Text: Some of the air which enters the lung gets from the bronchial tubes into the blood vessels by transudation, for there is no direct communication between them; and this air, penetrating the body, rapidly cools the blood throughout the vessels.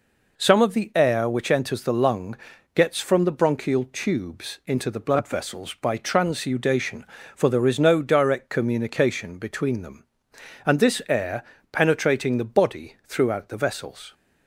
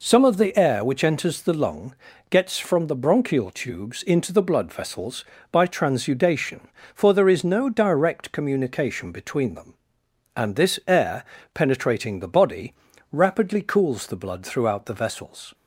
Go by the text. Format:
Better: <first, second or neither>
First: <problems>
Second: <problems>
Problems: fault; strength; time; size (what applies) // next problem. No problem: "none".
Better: second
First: pauses between "lung" and "gets"; at 2.3 s; 0.40 s long // skips "rapidly cools the blood"; at 13.0 s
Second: pauses between "lung" and "gets"; at 1.9 s; 0.38 s long